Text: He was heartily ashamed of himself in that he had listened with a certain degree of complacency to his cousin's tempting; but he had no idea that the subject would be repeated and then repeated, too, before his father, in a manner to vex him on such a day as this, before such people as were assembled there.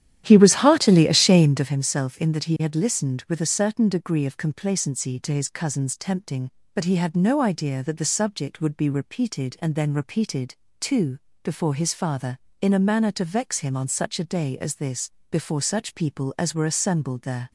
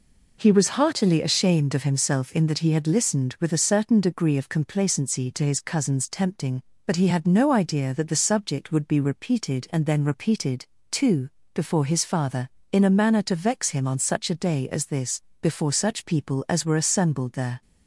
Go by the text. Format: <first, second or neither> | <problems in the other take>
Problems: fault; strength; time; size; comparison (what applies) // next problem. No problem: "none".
second | starts louder than the rest; strong; until 1.7 s; 11 dB